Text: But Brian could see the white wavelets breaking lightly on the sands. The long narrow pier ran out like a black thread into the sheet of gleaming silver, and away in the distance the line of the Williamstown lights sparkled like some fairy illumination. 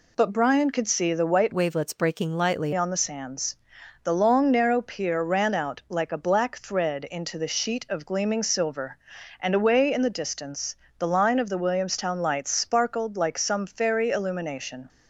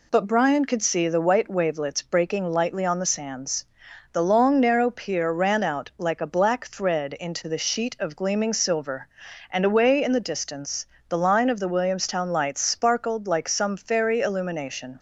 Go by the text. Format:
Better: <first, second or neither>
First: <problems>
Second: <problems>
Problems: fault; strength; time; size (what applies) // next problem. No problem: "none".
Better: second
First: changes voice from "wavelets" to "lightly"; from 1.5 to 2.7 s; 1.2 s long // pauses between "distance" and "the"; slight; at 10.7 s; 0.22 s long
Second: pauses between "distance" and "the"; slight; at 10.8 s; 0.22 s long